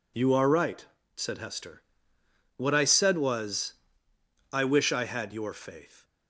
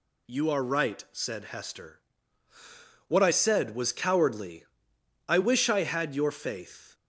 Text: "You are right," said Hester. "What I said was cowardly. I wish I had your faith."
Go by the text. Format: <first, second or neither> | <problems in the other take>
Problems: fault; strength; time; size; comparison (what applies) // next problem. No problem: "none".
second | skips "cowardly"; at 4.1 s